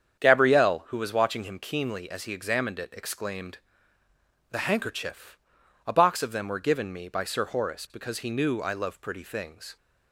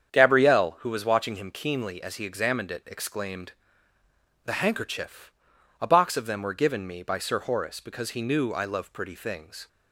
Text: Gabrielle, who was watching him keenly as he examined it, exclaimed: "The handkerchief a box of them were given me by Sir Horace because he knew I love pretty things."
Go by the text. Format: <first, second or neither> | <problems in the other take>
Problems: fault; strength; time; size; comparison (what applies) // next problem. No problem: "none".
neither | starts louder than the rest; strong; the same in both // pauses between "handkerchief" and "a"; noticeable; the same in both